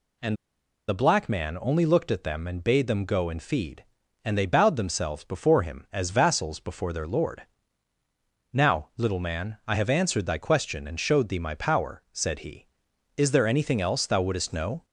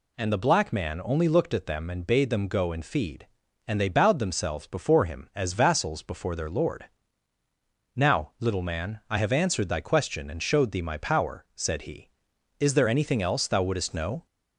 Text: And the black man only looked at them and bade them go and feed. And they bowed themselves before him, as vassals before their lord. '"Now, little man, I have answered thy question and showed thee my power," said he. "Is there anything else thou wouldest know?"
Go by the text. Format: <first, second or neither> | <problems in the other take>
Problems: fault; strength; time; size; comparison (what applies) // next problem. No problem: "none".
second | pauses between "And" and "the"; noticeable; at 0.3 s; 0.52 s long